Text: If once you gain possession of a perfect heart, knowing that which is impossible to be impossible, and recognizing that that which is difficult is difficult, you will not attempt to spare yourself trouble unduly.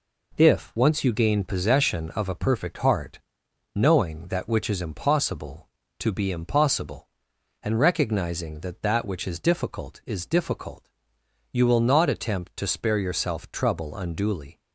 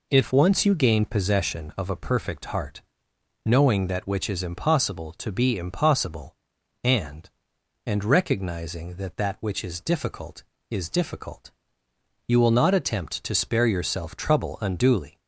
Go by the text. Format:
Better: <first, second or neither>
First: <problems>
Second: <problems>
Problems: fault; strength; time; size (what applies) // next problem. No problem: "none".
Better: first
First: none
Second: says "and" twice; at 7.8 s